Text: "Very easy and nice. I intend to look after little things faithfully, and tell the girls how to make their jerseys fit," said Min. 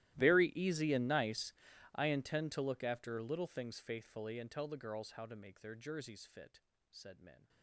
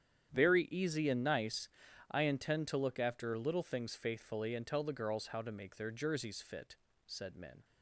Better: second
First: gets quieter; strong; throughout; 27 dB // starts louder than the rest; strong; until 1.2 s; 15 dB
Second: starts louder than the rest; strong; until 1.3 s; 9.5 dB

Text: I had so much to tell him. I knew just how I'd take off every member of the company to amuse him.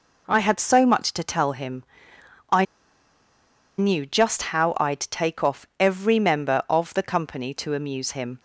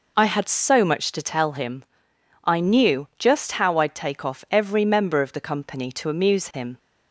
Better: second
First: pauses between "I" and "knew"; at 2.6 s; 1.1 s long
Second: none

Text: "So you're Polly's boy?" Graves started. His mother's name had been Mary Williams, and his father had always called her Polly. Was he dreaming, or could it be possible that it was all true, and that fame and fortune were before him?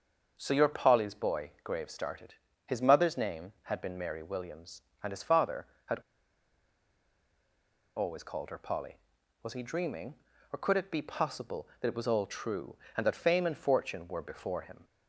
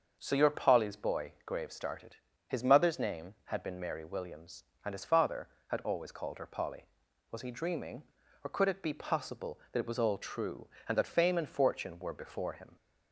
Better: second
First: starts louder than the rest; until 1.3 s; 6.5 dB // pauses between "had" and "always"; strong; at 5.9 s; 1.9 s long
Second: starts louder than the rest; until 1.2 s; 6.5 dB

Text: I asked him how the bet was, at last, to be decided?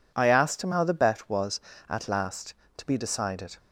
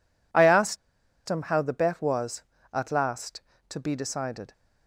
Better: first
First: none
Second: pauses between "asked" and "him"; noticeable; at 0.7 s; 0.51 s long

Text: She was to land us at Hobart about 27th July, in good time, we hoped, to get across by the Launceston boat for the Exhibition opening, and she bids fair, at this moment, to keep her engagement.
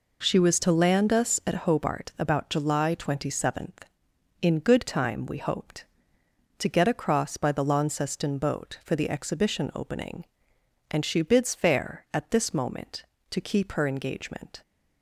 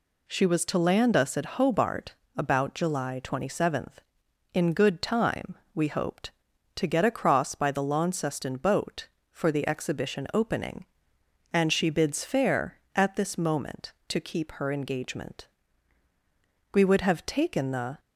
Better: first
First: none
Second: pauses between "Hobart" and "about"; slight; at 2.1 s; 0.22 s long // goes on to say "We would have taken the"; noticeable; from 16.7 s on; 1.2 s long

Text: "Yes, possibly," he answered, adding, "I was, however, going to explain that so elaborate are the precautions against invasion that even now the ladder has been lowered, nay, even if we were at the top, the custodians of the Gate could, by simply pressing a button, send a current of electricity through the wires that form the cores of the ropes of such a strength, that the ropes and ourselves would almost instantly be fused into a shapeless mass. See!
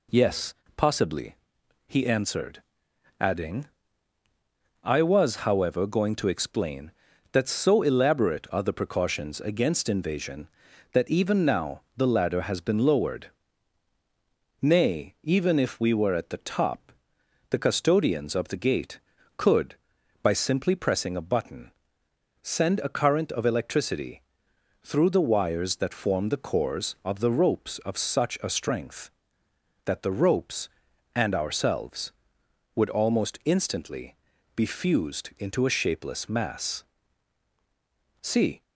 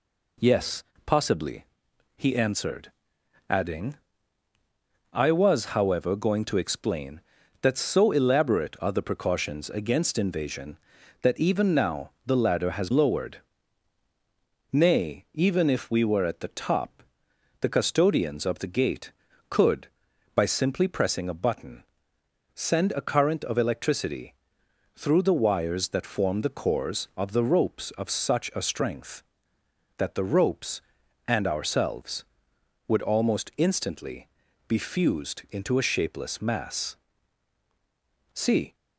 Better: first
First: pauses between "electricity" and "through"; noticeable; at 24.2 s; 0.60 s long // pauses between "instantly" and "be"; at 34.1 s; 0.40 s long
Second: skips "been"; at 12.8 s // pauses between "electricity" and "through"; noticeable; at 24.3 s; 0.60 s long // pauses between "instantly" and "be"; at 34.2 s; 0.40 s long

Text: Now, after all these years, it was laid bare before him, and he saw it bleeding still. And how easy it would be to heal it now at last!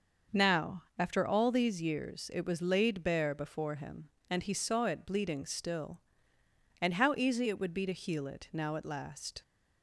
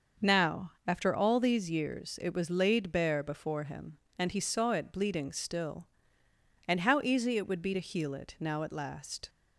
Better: neither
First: starts louder than the rest; until 1.4 s; 6 dB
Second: starts louder than the rest; noticeable; until 1.3 s; 6 dB

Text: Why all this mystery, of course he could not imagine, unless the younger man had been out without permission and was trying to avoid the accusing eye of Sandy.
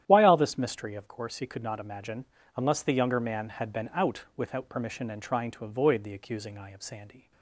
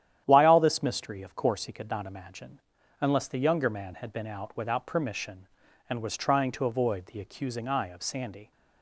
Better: second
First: starts louder than the rest; strong; until 1.0 s; 11 dB // skips "was"; at 5.2 s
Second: starts louder than the rest; strong; until 1.2 s; 10.5 dB

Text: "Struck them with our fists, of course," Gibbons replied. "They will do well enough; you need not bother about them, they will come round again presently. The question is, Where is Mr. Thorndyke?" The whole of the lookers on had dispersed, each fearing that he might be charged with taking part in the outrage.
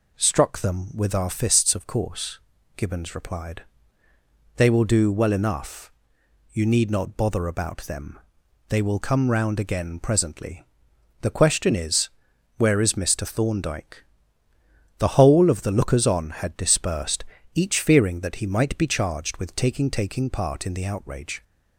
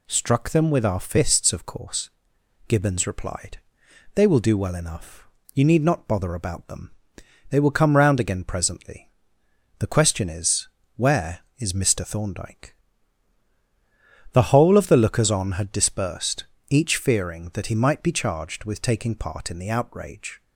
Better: second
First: says "taking" twice; at 19.8 s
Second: none

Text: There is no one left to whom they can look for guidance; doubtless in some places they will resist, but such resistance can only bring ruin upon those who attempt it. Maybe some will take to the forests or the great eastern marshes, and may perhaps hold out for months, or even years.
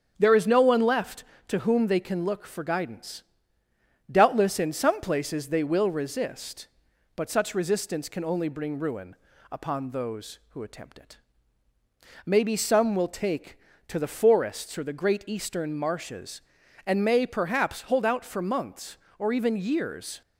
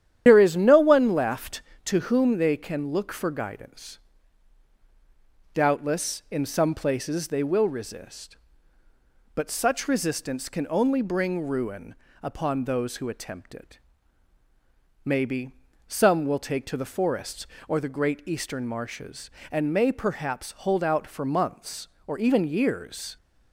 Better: first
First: starts louder than the rest; strong; until 1.1 s; 8 dB // pauses between "ruin" and "upon"; slight; at 9.1 s; 0.34 s long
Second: loses the start of "There"; at 0.2 s; 75 ms // starts louder than the rest; strong; until 1.2 s; 10.5 dB // pauses between "ruin" and "upon"; slight; at 11.9 s; 0.28 s long // pauses between "Maybe" and "some"; at 15.5 s; 0.38 s long

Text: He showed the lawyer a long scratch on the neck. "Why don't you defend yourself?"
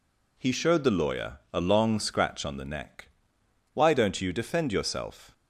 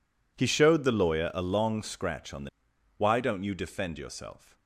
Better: first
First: none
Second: skips "neck"; at 2.7 s

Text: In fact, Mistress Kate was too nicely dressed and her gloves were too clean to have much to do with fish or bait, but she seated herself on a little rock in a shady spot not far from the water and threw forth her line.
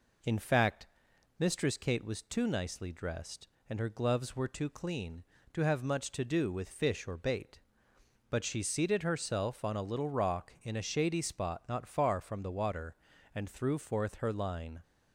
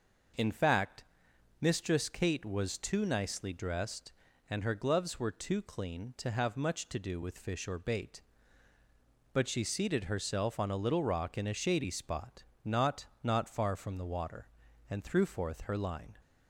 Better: first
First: none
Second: pauses between "spot" and "not"; slight; at 12.4 s; 0.22 s long // says "not" twice; at 13.2 s

